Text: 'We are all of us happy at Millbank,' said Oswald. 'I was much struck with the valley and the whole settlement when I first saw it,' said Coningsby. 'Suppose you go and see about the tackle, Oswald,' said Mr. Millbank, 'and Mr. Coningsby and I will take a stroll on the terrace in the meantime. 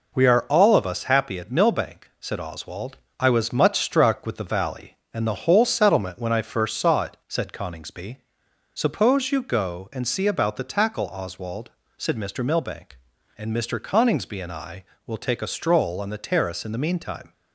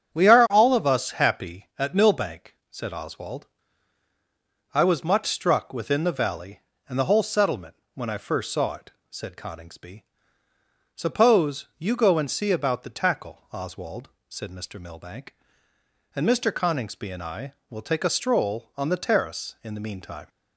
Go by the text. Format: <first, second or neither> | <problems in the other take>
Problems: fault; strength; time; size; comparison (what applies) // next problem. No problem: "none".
first | starts louder than the rest; strong; until 1.1 s; 8.5 dB // says "within" for "with"; at 5.7 s // pauses between "settlement" and "when"; slight; at 7.7 s; 0.20 s long